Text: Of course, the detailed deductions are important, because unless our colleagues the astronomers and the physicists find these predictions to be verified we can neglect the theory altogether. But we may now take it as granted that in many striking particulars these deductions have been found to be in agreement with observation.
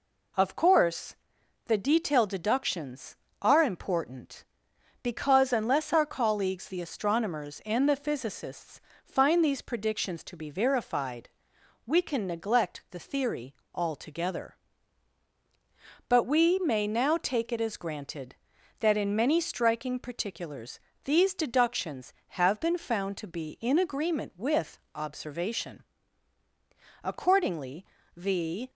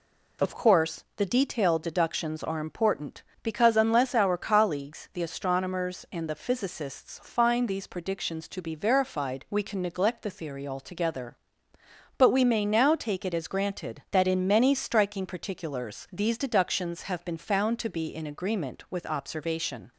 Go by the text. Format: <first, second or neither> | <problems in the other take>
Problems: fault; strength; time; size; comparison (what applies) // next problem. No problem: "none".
second | pauses between "physicists" and "find"; slight; at 8.7 s; 0.24 s long // pauses between "verified" and "we"; noticeable; at 11.2 s; 0.58 s long // pauses between "theory" and "altogether"; slight; at 13.5 s; 0.20 s long // pauses between "particulars" and "these"; slight; at 20.7 s; 0.24 s long // pauses between "with" and "observation"; slight; at 24.7 s; 0.18 s long // goes on to say "Accordingly the"; from 27.0 s on; 1.6 s long